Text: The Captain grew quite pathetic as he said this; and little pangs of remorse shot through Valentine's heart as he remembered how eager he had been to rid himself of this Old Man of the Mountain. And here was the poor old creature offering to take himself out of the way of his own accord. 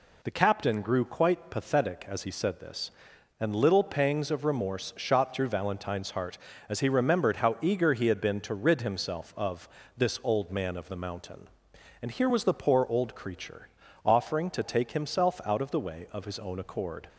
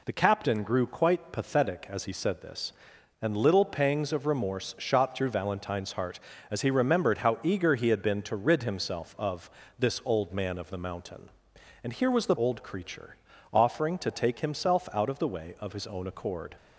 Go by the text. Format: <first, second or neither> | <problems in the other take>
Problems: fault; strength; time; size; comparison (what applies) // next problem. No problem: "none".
first | pauses between "of" and "this"; slight; at 9.4 s; 0.30 s long; slight in the first // skips "poor"; at 12.3 s // pauses between "creature" and "offering"; slight; at 13.1 s; 0.36 s long; slight in the first